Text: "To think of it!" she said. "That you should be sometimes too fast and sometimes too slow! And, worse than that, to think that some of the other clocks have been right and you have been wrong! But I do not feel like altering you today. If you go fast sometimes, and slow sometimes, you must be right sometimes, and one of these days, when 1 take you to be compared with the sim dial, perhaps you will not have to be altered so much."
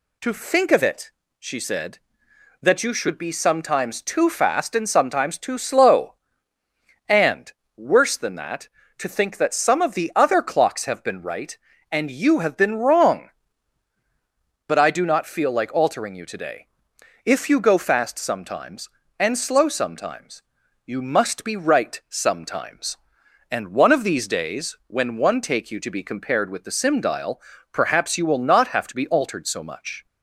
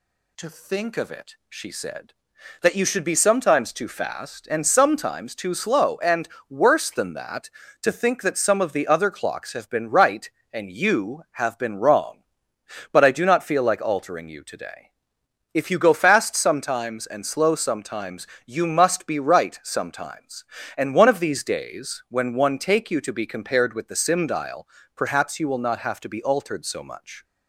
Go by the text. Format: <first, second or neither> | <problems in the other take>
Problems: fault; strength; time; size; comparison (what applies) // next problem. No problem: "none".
neither | none